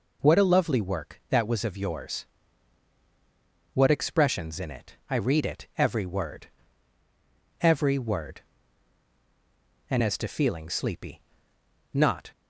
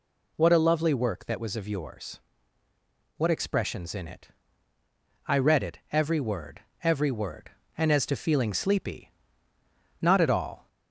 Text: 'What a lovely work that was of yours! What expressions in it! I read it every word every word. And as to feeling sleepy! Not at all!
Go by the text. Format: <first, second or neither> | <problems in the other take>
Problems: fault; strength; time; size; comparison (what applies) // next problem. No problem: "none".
second | pauses between "word" and "every"; at 6.4 s; 1.1 s long; slight in the second // stops before "at all"; at 12.3 s